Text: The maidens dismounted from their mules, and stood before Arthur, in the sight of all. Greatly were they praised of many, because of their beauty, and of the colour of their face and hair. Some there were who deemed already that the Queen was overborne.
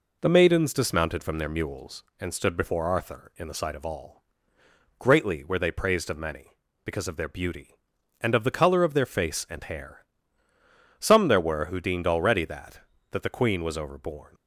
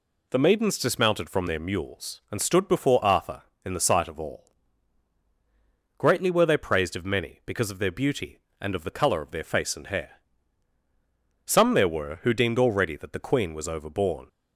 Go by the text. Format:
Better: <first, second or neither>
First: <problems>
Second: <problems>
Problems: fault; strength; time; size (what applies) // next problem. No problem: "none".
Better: second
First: says "that" twice; at 13.1 s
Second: none